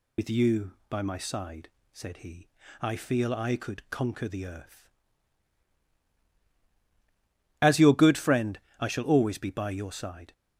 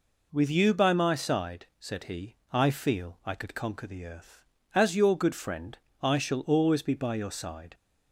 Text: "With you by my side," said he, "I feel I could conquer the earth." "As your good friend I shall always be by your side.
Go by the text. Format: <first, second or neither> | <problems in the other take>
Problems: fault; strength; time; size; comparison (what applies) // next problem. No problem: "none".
second | loses the start of "With"; at 0.1 s; 60 ms // pauses between "friend" and "I"; slight; at 8.5 s; 0.22 s long; slight in the second